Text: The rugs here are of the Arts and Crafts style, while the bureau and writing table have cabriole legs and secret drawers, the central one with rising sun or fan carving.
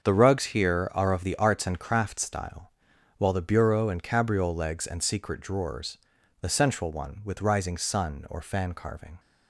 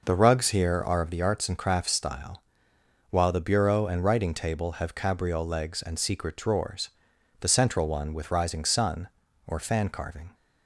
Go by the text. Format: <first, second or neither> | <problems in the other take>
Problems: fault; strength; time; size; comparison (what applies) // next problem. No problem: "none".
second | starts louder than the rest; until 1.0 s; 6.5 dB // skips "writing table have"; at 4.0 s